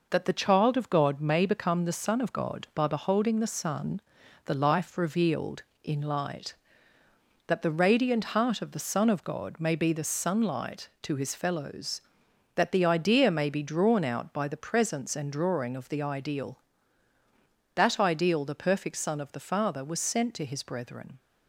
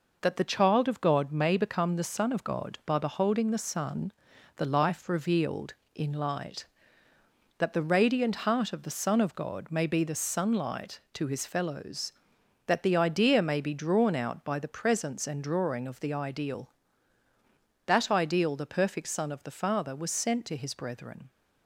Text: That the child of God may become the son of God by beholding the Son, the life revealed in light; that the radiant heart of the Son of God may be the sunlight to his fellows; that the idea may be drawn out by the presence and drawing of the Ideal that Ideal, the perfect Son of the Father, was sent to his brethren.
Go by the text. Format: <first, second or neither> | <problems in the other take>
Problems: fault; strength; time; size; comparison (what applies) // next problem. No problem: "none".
neither | none